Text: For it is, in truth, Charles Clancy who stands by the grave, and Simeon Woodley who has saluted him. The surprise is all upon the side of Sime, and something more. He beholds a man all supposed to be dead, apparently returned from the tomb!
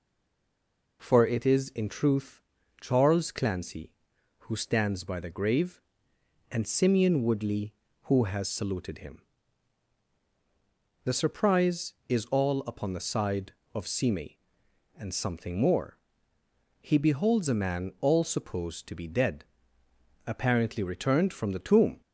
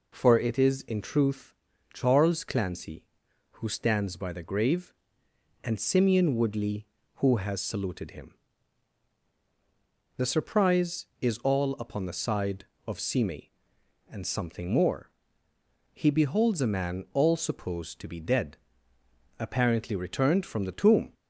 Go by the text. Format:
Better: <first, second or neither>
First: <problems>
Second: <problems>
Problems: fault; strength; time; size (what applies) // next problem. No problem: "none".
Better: second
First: stays silent before the first word; until 1.0 s; 1.0 s long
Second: none